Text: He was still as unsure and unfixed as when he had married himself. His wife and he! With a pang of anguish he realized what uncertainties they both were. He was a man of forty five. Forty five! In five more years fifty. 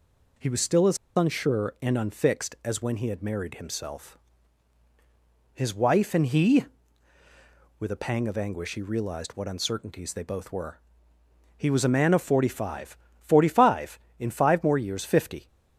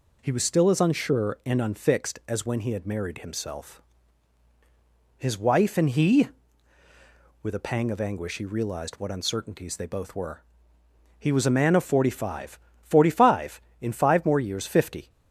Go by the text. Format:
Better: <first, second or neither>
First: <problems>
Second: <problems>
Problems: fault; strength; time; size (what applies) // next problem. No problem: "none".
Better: second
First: pauses between "as" and "unsure"; slight; at 0.9 s; 0.19 s long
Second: none